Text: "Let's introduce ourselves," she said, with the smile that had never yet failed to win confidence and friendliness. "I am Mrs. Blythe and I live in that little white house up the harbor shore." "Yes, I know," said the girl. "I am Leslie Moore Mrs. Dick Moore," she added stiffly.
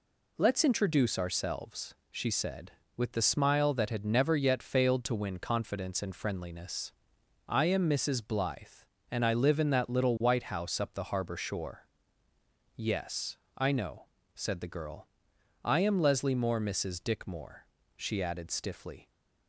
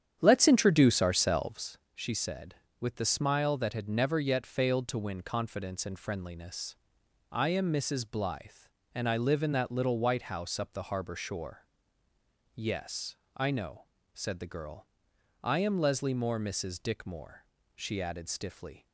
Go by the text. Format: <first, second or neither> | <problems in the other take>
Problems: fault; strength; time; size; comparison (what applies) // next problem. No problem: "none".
first | starts louder than the rest; strong; until 1.7 s; 9 dB